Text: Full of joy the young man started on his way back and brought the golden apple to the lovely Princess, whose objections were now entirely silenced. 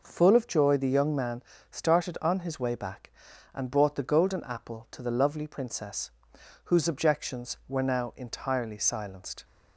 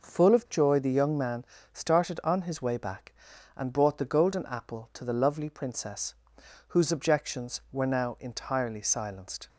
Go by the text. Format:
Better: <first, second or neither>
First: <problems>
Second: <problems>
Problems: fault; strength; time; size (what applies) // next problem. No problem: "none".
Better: neither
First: pauses between "man" and "started"; slight; at 1.4 s; 0.26 s long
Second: pauses between "man" and "started"; slight; at 1.4 s; 0.26 s long